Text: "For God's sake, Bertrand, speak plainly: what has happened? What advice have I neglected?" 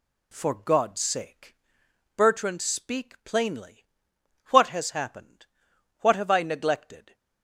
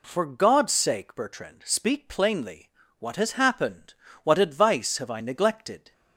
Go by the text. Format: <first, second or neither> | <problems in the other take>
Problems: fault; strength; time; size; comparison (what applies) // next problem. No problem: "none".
second | skips "advice"; at 6.1 s